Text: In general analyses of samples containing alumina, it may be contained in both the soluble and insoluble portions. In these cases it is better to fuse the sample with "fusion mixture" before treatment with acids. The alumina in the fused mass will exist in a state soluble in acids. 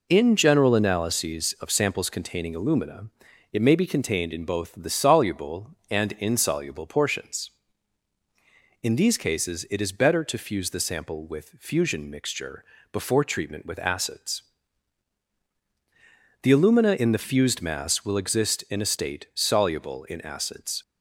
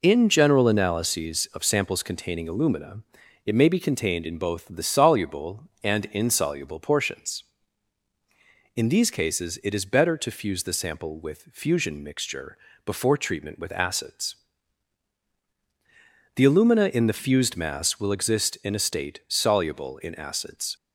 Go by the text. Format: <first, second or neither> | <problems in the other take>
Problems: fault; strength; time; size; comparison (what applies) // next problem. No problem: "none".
neither | pauses between "mixture" and "before"; slight; the same in both